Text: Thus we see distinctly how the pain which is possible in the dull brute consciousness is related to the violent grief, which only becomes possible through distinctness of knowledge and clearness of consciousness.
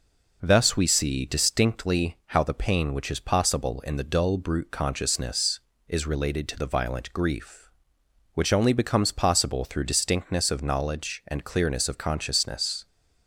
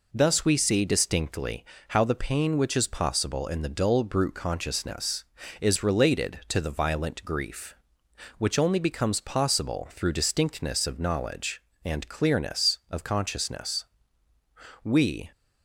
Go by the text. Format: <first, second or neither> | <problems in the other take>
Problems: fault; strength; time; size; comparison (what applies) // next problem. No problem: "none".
first | pauses between "distinctly" and "how"; slight; at 1.6 s; 0.24 s long // goes on to say "We"; slight; from 14.8 s on; 0.48 s long